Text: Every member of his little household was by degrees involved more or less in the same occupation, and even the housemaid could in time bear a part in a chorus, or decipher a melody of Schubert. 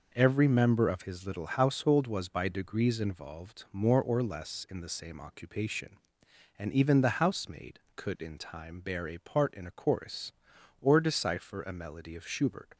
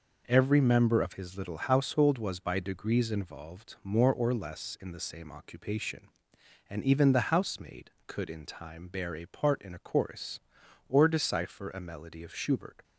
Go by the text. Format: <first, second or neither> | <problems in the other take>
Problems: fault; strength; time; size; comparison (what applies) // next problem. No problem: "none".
neither | none